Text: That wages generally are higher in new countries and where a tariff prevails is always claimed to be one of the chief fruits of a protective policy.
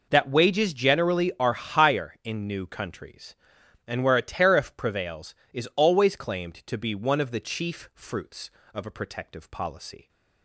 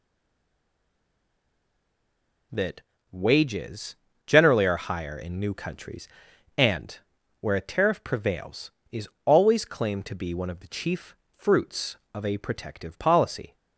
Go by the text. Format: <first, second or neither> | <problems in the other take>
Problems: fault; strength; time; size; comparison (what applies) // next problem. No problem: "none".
first | stays silent before the first word; until 2.5 s; 2.5 s long // pauses between "That" and "wages"; slight; at 2.7 s; 0.32 s long // pauses between "wages" and "generally"; slight; at 3.9 s; 0.30 s long // pauses between "and" and "where"; at 6.9 s; 0.42 s long // pauses between "is" and "always"; slight; at 9.0 s; 0.18 s long // pauses between "chief" and "fruits"; slight; at 11.1 s; 0.22 s long